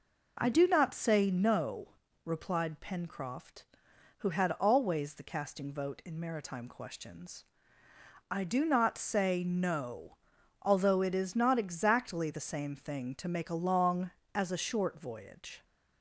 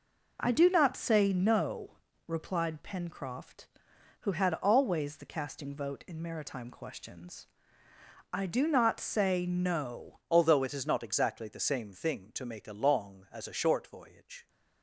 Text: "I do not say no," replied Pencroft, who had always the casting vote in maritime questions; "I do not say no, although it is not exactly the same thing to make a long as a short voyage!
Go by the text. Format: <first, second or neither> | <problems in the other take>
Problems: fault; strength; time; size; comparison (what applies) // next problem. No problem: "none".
first | changes voice at "although"; from 10.2 s on; 4.2 s long